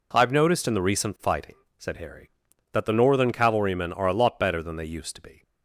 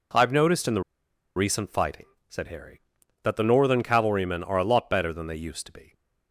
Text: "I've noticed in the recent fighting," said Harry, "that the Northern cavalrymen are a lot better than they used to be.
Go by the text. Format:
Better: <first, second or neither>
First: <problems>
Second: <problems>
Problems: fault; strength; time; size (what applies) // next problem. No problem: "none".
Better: first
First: none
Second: pauses between "the" and "recent"; noticeable; at 0.8 s; 0.54 s long